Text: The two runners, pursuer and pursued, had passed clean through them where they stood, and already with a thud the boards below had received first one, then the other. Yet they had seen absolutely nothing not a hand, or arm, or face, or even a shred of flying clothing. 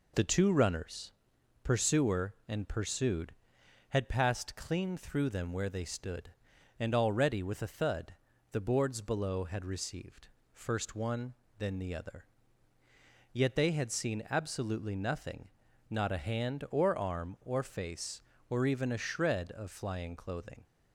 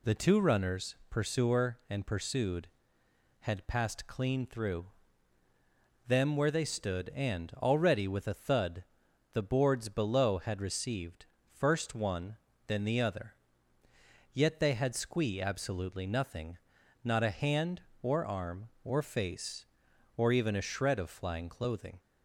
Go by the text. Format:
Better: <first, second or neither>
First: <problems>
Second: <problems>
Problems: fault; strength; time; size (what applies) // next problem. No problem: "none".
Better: first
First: pauses between "thud" and "the"; at 8.1 s; 0.38 s long // pauses between "received" and "first"; slight; at 10.2 s; 0.24 s long // pauses between "nothing" and "not"; at 15.4 s; 0.42 s long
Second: pauses between "through" and "them"; at 4.8 s; 1.2 s long // pauses between "thud" and "the"; noticeable; at 8.8 s; 0.50 s long // pauses between "received" and "first"; slight; at 11.2 s; 0.24 s long // says "squee" for "seen"; at 14.9 s // pauses between "nothing" and "not"; noticeable; at 16.5 s; 0.46 s long